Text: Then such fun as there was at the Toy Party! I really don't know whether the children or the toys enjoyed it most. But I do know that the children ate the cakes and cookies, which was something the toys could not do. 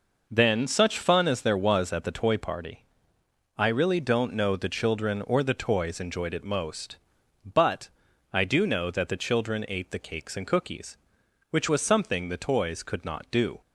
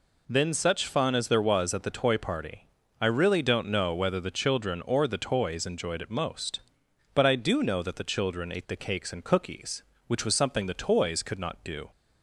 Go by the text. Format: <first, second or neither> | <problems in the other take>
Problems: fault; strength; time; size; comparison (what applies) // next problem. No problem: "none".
second | skips "whether"; at 4.5 s // pauses between "But" and "I"; at 7.8 s; 0.44 s long